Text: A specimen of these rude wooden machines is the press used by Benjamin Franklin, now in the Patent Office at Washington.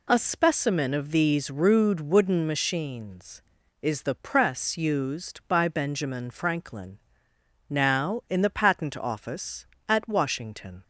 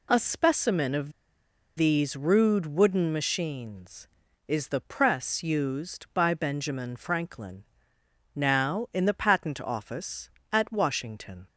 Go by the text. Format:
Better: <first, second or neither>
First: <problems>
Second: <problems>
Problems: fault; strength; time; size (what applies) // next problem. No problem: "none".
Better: first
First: none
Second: pauses between "of" and "these"; noticeable; at 1.1 s; 0.65 s long